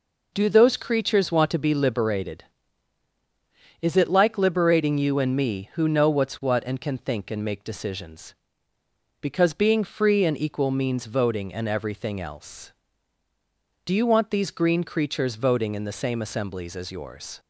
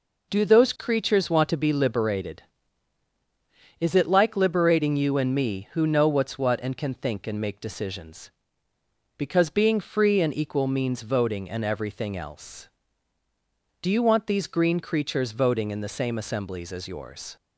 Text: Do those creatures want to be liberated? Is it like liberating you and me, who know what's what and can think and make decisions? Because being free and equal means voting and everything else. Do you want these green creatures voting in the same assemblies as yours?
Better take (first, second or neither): neither